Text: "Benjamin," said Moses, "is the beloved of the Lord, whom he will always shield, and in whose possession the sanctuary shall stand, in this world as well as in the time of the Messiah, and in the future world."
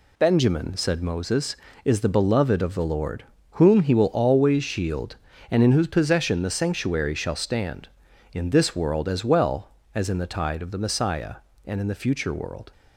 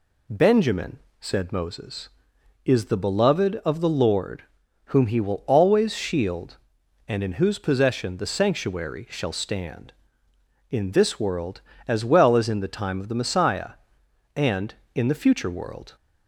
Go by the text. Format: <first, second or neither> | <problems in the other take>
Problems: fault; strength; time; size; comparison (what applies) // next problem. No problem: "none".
second | says "tide" for "time"; at 10.2 s